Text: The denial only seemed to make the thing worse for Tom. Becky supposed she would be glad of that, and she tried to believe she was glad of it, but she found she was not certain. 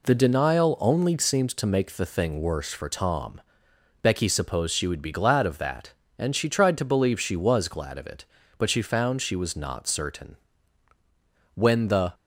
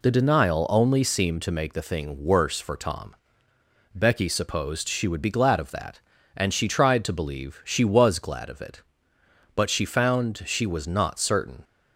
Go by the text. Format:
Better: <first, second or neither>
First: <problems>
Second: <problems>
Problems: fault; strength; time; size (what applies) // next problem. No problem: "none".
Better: second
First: goes on to say "When the"; from 11.5 s on; 0.60 s long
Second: none